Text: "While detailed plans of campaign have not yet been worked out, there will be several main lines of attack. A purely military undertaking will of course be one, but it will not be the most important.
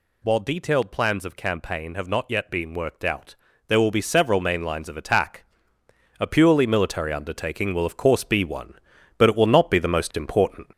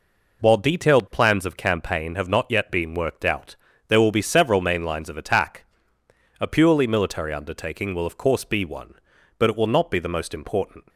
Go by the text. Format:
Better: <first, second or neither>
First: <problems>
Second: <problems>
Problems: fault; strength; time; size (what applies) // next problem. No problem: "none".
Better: second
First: gets louder; throughout; 4 dB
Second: none